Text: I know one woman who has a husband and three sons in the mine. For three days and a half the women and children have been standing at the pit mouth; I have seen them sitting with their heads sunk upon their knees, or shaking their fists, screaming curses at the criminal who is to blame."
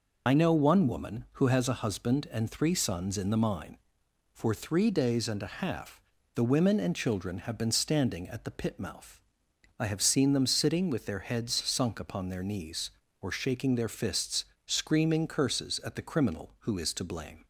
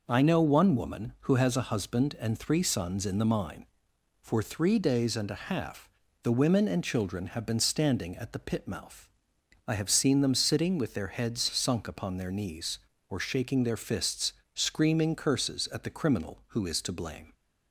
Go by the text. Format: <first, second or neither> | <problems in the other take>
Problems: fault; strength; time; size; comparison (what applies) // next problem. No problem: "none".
second | loses the start of "I"; at 0.2 s; 70 ms // pauses between "half" and "the"; slight; at 6.0 s; 0.32 s long; slight in the second